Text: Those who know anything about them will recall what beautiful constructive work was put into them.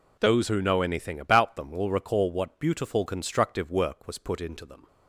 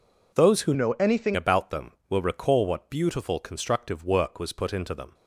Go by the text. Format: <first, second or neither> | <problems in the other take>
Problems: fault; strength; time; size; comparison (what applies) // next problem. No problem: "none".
first | changes voice from "know" to "anything"; from 0.7 to 1.3 s; 0.6 s long